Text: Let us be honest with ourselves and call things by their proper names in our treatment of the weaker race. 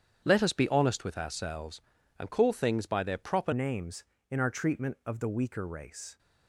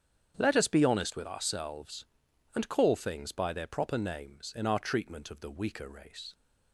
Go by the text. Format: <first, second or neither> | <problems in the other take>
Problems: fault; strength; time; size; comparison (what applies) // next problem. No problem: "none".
second | starts louder than the rest; strong; until 1.2 s; 8.5 dB; strong in the second // changes voice at "names"; from 3.5 s on; 2.6 s long